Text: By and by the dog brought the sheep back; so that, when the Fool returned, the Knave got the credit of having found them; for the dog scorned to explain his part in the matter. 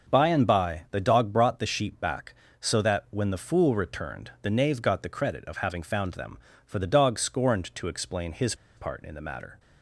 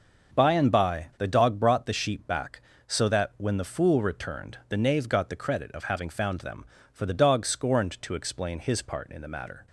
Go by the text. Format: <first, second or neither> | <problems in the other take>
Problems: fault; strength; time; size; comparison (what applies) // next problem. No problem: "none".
second | starts louder than the rest; until 1.1 s; 6.5 dB; also in the second // pauses between "his" and "part"; slight; at 8.5 s; 0.22 s long